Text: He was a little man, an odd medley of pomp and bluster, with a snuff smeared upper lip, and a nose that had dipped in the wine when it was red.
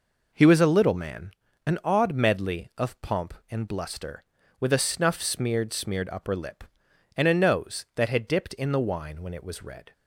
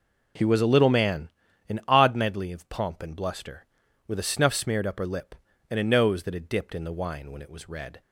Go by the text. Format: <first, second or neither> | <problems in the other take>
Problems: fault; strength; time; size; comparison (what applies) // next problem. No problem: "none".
second | says "smeared" twice; at 5.7 s